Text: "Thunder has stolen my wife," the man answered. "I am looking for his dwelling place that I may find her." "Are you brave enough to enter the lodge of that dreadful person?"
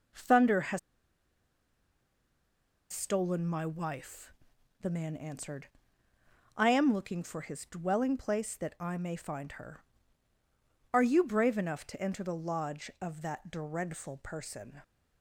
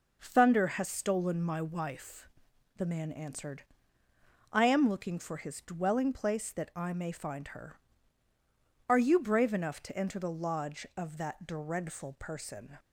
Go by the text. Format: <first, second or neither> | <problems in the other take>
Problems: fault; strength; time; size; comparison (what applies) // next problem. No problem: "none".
second | pauses between "has" and "stolen"; strong; at 0.7 s; 2.1 s long